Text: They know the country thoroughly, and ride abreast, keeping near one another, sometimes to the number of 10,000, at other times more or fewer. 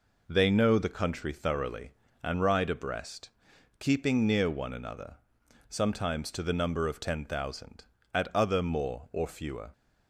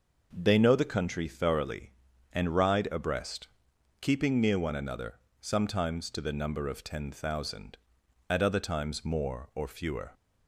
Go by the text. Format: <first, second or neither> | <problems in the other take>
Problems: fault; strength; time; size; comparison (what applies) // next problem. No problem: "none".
second | skips "times"; at 8.6 s